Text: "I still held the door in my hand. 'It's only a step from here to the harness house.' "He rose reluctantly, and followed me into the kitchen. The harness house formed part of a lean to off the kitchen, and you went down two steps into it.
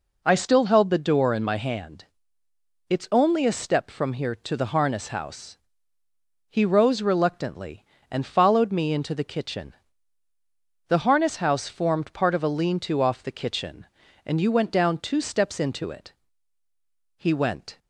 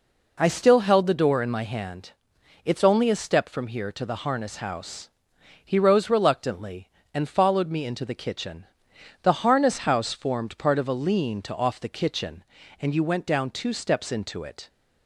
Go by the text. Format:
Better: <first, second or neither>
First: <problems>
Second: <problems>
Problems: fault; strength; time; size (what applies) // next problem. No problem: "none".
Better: second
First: goes on to say "He went"; noticeable; from 17.1 s on; 0.62 s long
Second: none